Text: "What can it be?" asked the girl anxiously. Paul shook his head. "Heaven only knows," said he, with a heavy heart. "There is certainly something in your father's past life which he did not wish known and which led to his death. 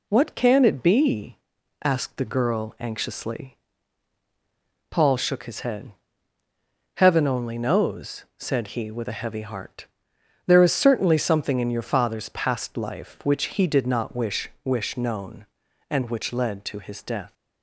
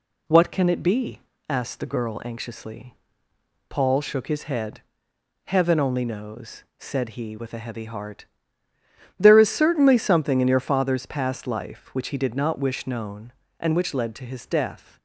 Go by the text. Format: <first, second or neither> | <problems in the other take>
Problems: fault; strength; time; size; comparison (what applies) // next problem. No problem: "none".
second | says "wish" twice; at 14.6 s